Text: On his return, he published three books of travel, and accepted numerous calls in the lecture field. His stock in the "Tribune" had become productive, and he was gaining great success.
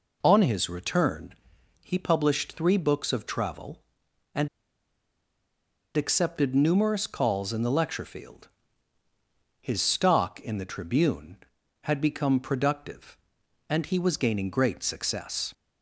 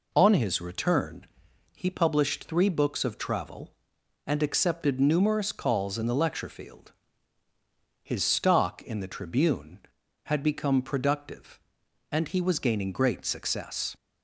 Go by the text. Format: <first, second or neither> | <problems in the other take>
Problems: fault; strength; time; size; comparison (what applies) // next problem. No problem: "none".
second | pauses between "and" and "accepted"; strong; at 4.4 s; 1.4 s long